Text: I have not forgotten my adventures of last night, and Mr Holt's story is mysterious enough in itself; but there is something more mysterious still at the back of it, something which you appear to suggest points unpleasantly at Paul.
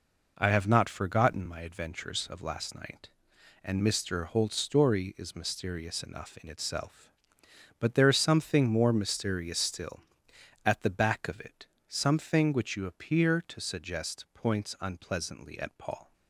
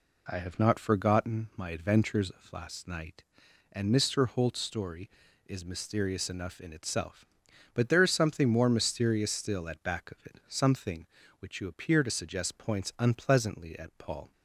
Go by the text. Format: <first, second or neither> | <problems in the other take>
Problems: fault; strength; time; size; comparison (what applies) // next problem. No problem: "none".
first | skips "the"; at 9.8 s